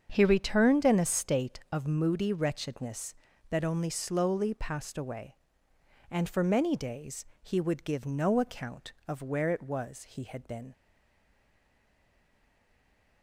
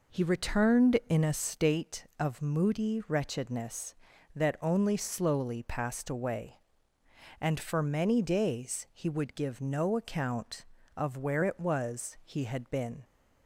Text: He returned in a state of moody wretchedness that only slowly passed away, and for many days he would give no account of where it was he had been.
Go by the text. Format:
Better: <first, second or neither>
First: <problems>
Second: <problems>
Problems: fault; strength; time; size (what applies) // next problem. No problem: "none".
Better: second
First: starts louder than the rest; until 1.1 s; 7 dB // pauses between "days" and "he"; slight; at 7.2 s; 0.16 s long // stays silent after the last word; from 10.7 s on; 2.5 s long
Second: none